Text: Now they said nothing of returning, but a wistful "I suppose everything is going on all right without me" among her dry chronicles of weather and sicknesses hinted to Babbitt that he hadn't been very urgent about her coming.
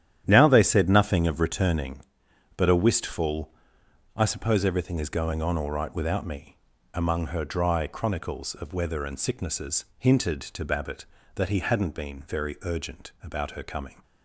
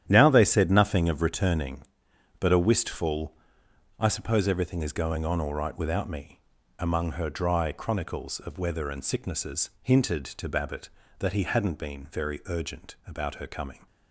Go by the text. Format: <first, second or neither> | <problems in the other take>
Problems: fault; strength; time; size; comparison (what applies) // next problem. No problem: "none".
neither | starts louder than the rest; strong; the same in both // pauses between "wistful" and "I"; noticeable; the same in both // pauses between "me" and "among"; the same in both